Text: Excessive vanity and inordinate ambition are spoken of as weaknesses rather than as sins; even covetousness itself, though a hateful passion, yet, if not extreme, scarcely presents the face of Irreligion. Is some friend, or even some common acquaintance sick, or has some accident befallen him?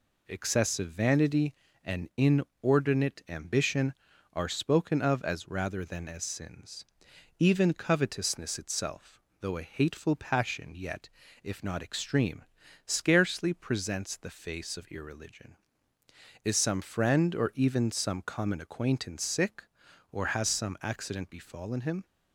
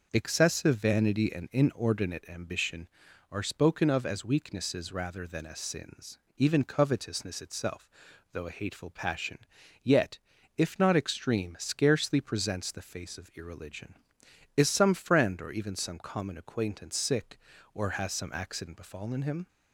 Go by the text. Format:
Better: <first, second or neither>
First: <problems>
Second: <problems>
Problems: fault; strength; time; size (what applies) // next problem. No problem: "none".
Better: second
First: skips "weaknesses"; at 5.4 s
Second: none